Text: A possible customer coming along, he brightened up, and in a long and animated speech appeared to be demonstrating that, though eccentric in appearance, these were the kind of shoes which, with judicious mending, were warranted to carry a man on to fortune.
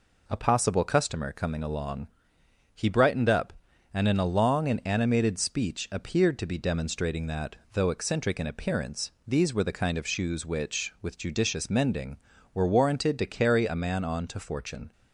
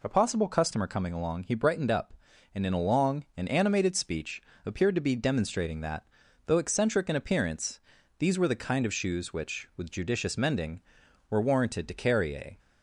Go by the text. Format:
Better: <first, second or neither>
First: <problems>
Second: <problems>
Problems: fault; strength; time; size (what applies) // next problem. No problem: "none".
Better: first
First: none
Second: pauses between "speech" and "appeared"; slight; at 4.4 s; 0.22 s long // stops before "man on to fortune"; at 12.5 s